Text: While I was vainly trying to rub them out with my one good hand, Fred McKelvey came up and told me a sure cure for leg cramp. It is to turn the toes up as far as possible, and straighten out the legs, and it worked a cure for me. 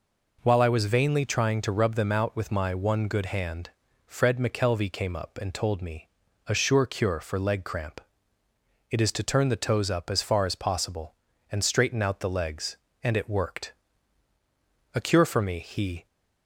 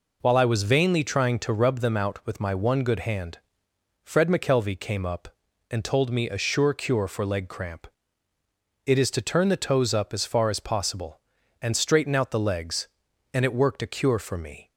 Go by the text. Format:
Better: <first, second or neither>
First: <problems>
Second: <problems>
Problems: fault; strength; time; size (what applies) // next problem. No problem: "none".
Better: second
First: pauses between "me" and "a"; at 6.0 s; 0.40 s long // pauses between "worked" and "a"; at 13.7 s; 1.2 s long // goes on to say "He"; slight; from 15.5 s on; 0.46 s long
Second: none